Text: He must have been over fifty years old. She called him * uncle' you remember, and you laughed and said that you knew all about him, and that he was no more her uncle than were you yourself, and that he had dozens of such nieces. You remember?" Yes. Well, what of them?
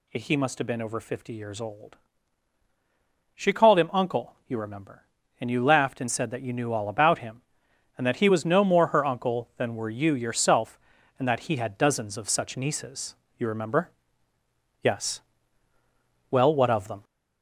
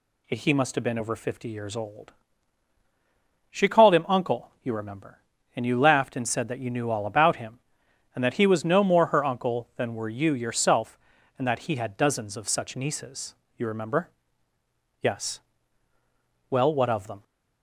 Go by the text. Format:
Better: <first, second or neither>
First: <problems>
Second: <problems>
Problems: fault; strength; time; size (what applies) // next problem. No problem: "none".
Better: second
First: gets louder; noticeable; throughout; 4.5 dB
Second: none